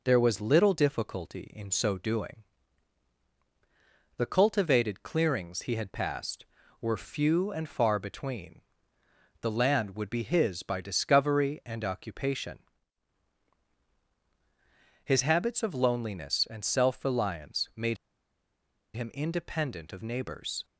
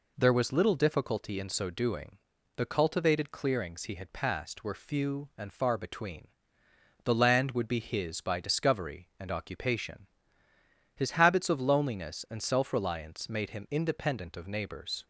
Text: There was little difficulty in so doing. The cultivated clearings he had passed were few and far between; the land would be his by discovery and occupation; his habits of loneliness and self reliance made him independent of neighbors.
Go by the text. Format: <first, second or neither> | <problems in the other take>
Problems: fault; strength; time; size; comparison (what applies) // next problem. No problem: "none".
second | pauses between "made" and "him"; at 17.9 s; 0.99 s long